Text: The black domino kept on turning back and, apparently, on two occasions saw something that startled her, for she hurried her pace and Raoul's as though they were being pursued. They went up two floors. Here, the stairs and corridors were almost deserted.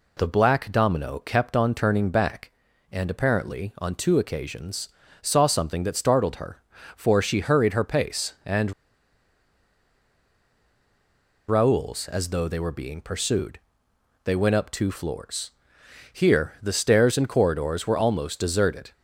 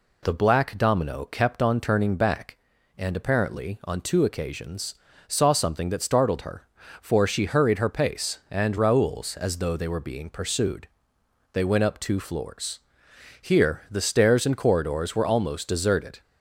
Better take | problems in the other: second | pauses between "occasions" and "saw"; slight; at 4.8 s; 0.32 s long; slight in the second // pauses between "and" and "Raoul's"; strong; at 8.7 s; 2.7 s long

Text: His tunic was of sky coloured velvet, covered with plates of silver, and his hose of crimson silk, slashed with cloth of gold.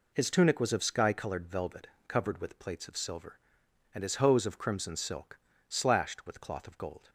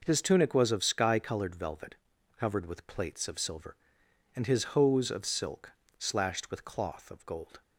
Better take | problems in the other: first | skips "crimson"; at 5.2 s

